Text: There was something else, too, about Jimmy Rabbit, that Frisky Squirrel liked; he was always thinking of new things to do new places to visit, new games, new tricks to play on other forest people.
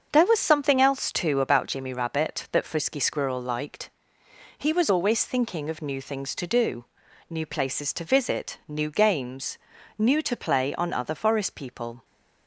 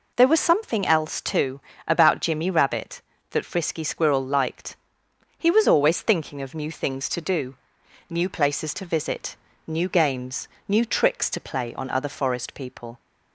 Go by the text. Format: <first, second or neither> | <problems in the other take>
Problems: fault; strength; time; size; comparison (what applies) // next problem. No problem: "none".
second | starts louder than the rest; until 1.1 s; 7 dB // pauses between "do" and "new"; at 6.8 s; 0.44 s long; noticeable in the second // skips "tricks"; at 10.2 s